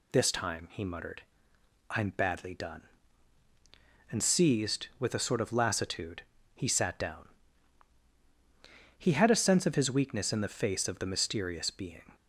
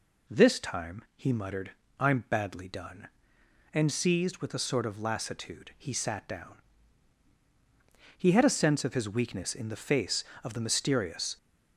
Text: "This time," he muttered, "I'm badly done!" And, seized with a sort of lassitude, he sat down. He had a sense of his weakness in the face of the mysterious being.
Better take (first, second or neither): first